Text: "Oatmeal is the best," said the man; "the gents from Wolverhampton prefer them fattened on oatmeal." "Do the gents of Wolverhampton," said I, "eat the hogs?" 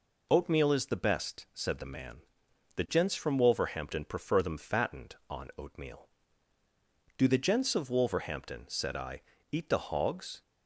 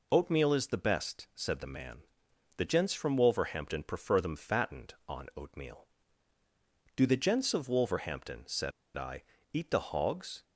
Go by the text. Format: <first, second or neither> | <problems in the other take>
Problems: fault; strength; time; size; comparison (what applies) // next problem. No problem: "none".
first | pauses between "said" and "I"; slight; at 8.7 s; 0.23 s long